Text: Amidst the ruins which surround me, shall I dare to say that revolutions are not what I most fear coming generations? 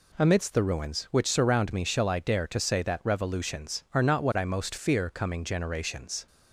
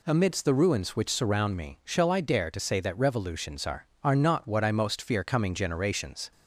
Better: first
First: none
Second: says "are" twice; at 4.0 s

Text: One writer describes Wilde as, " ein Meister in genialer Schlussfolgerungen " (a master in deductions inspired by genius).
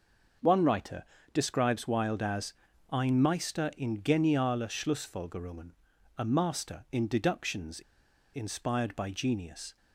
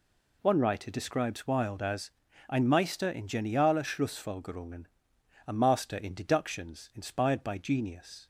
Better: second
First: starts louder than the rest; until 1.7 s; 6 dB // pauses between "writer" and "describes"; slight; at 1.0 s; 0.30 s long // pauses between "deductions" and "inspired"; noticeable; at 7.8 s; 0.52 s long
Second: none

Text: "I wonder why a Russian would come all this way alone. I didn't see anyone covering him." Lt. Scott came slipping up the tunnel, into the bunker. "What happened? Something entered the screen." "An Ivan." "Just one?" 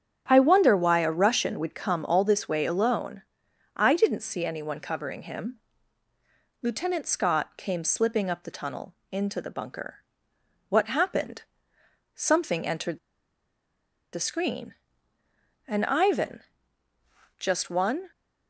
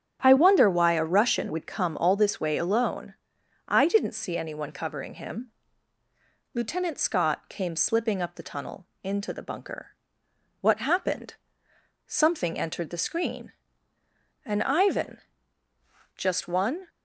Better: second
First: starts louder than the rest; strong; until 1.2 s; 9 dB // pauses between "entered" and "the"; at 12.9 s; 1.1 s long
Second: starts louder than the rest; strong; until 1.2 s; 9.5 dB

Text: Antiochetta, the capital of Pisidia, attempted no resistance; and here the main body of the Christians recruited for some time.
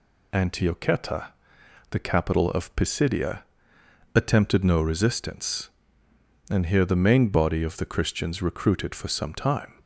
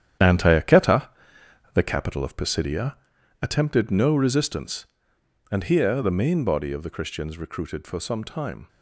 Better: first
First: none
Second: gets quieter; strong; throughout; 9.5 dB

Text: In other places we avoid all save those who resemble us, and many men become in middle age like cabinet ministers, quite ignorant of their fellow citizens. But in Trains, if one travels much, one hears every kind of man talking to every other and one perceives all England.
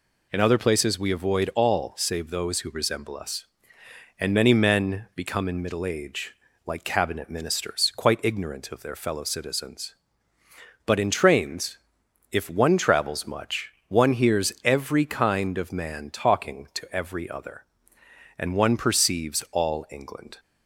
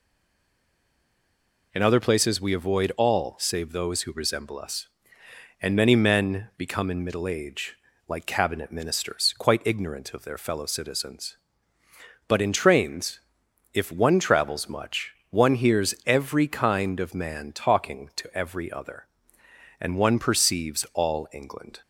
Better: first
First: pauses between "age" and "like"; slight; at 6.3 s; 0.32 s long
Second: stays silent before the first word; noticeable; until 1.7 s; 1.7 s long // pauses between "age" and "like"; slight; at 7.7 s; 0.32 s long

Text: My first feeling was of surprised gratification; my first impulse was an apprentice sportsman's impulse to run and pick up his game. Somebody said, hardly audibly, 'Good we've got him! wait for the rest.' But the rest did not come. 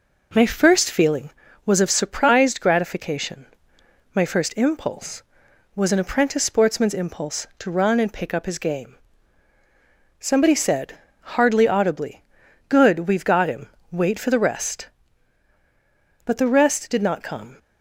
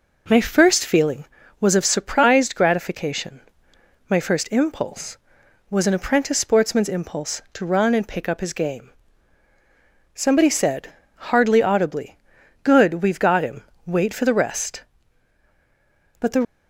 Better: first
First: none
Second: stops before "rest did not come"; at 16.4 s

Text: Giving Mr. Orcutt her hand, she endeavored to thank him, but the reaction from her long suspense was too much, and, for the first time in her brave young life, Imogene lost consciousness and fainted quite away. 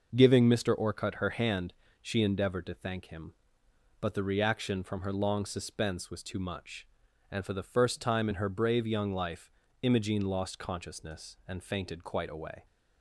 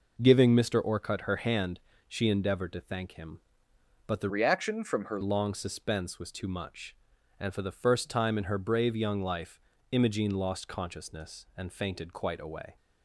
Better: first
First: none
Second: changes voice from "reaction" to "her"; from 4.2 to 5.1 s; 0.9 s long

